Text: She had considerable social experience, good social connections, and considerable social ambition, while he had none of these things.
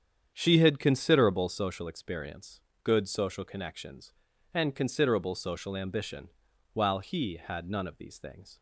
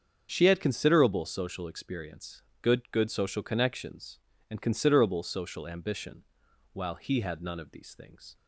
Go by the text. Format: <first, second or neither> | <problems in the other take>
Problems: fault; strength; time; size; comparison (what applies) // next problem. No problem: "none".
first | starts louder than the rest; strong; until 1.3 s; 7 dB; strong in the first // says "good" twice; at 2.9 s